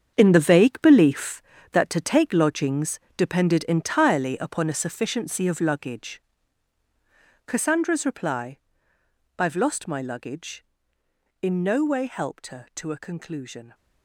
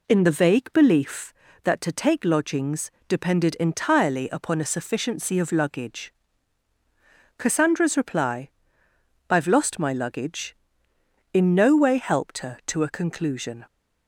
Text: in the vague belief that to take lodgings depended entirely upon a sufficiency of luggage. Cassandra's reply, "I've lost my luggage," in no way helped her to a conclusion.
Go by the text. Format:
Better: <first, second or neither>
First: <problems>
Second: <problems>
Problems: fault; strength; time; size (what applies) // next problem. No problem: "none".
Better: second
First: gets quieter; strong; throughout; 11.5 dB // pauses between "lodgings" and "depended"; slight; at 2.9 s; 0.18 s long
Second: pauses between "lodgings" and "depended"; slight; at 2.9 s; 0.18 s long